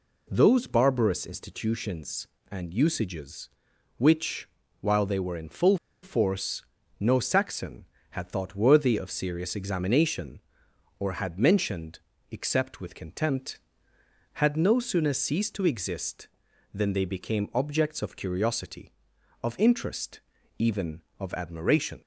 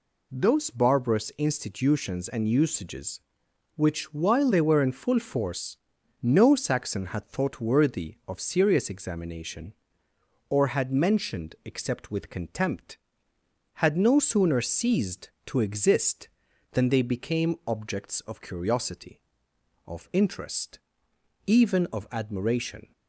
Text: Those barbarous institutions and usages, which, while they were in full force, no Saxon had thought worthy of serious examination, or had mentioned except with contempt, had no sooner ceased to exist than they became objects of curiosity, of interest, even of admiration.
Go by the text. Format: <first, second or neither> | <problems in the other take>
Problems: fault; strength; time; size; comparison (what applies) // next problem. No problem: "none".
second | pauses between "full" and "force"; slight; at 5.7 s; 0.26 s long // pauses between "mentioned" and "except"; slight; at 12.0 s; 0.30 s long